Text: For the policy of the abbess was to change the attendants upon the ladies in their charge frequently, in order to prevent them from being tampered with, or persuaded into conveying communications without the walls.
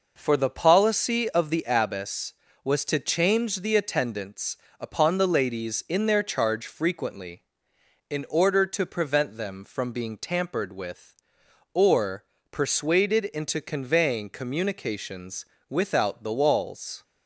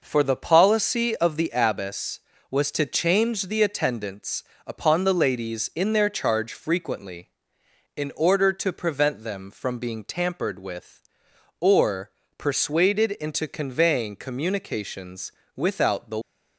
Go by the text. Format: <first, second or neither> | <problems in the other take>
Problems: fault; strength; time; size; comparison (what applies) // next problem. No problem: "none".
first | pauses between "attendants" and "upon"; slight; at 4.4 s; 0.24 s long; slight in the first // pauses between "or" and "persuaded"; slight; at 12.1 s; 0.26 s long; slight in the first // pauses between "communications" and "without"; slight; at 15.3 s; 0.24 s long; slight in the first // stops before "walls"; at 16.2 s